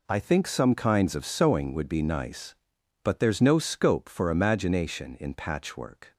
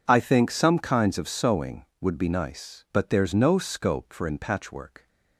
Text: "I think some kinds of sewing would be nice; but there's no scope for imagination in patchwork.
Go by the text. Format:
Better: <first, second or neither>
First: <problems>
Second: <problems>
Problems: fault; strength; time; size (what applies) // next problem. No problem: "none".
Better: first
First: none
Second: skips "imagination"; at 4.2 s